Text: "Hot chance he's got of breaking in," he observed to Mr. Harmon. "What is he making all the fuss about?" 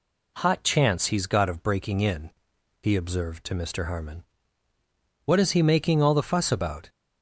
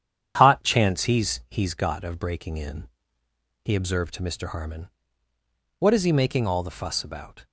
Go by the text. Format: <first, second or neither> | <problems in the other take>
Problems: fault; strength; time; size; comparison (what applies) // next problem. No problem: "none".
first | starts louder than the rest; strong; until 1.3 s; 9 dB // says "he's" twice; at 1.4 s